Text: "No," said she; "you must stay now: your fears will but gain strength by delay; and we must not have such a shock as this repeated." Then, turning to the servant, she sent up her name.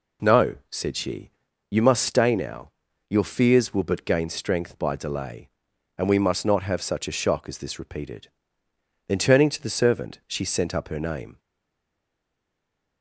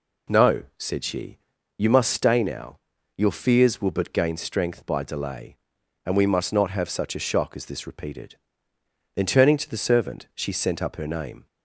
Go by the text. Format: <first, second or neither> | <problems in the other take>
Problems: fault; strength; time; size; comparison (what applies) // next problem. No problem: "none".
second | stays silent after the last word; noticeable; from 11.3 s on; 1.7 s long